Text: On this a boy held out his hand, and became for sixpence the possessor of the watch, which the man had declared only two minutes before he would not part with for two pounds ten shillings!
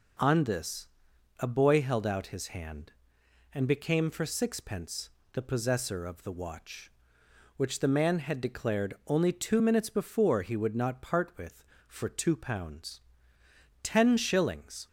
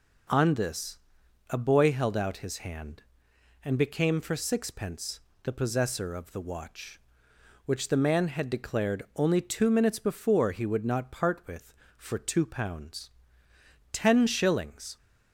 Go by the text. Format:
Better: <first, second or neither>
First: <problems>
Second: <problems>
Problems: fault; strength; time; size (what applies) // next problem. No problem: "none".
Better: neither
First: pauses between "this" and "a"; noticeable; at 0.8 s; 0.50 s long // pauses between "sixpence" and "the"; slight; at 5.0 s; 0.24 s long // pauses between "pounds" and "ten"; noticeable; at 13.0 s; 0.82 s long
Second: pauses between "this" and "a"; noticeable; at 0.9 s; 0.50 s long // pauses between "sixpence" and "the"; slight; at 5.2 s; 0.24 s long // pauses between "pounds" and "ten"; noticeable; at 13.1 s; 0.82 s long